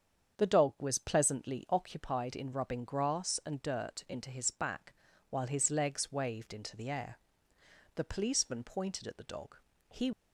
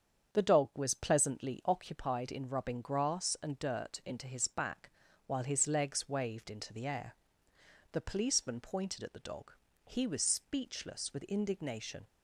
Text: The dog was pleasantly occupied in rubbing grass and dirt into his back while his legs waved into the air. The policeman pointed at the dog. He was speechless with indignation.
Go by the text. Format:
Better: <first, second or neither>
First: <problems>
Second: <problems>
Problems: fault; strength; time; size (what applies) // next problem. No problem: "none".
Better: second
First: starts louder than the rest; strong; until 1.4 s; 7.5 dB // pauses between "back" and "while"; at 4.9 s; 0.38 s long // stops before "was speechless with indignation"; at 10.1 s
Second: starts louder than the rest; strong; until 1.4 s; 7.5 dB // pauses between "back" and "while"; at 4.8 s; 0.38 s long